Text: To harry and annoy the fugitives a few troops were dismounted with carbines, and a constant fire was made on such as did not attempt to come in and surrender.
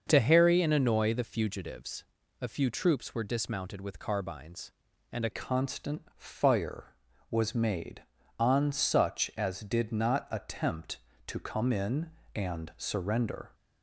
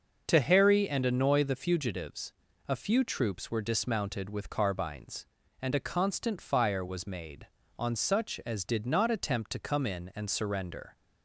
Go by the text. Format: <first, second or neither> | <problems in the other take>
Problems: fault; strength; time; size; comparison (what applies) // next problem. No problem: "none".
second | starts louder than the rest; until 1.0 s; 6.5 dB // pauses between "fugitives" and "a"; slight; at 2.0 s; 0.34 s long; slight in the second // changes voice at "constant"; from 5.3 s on; 8.2 s long